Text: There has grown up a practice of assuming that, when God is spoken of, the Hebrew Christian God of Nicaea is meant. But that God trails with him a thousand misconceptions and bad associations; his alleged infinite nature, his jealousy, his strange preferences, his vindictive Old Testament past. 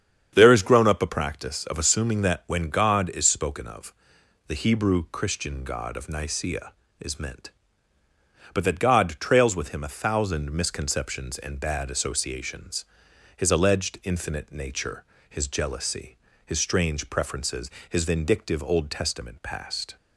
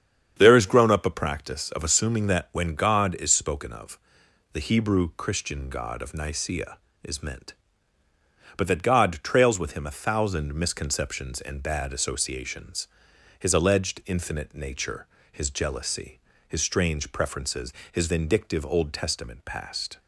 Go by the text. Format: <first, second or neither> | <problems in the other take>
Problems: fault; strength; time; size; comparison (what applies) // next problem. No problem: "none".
neither | starts louder than the rest; strong; the same in both